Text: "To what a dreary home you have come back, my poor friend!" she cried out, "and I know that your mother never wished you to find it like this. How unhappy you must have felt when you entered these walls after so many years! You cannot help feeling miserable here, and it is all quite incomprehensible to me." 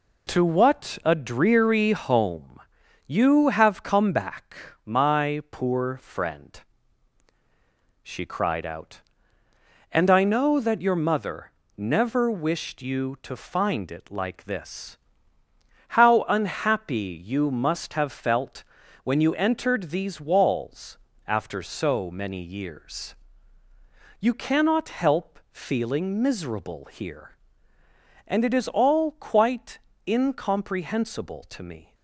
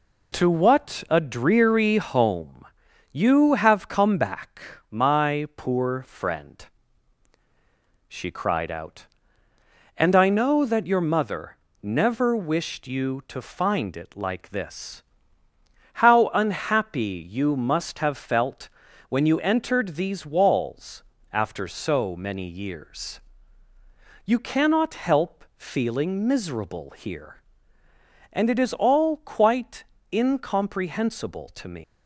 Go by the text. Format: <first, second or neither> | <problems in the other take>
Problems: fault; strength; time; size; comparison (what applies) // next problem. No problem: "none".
first | pauses between "home" and "you"; noticeable; at 2.6 s; 0.46 s long; noticeable in the first // pauses between "mother" and "never"; slight; at 11.5 s; 0.26 s long; slight in the first // pauses between "felt" and "when"; at 18.6 s; 0.40 s long; also in the first // pauses between "walls" and "after"; slight; at 21.0 s; 0.28 s long; slight in the first // pauses between "quite" and "incomprehensible"; slight; at 29.8 s; 0.32 s long; slight in the first // leaves "me" unfinished; at 31.8 s; 150 ms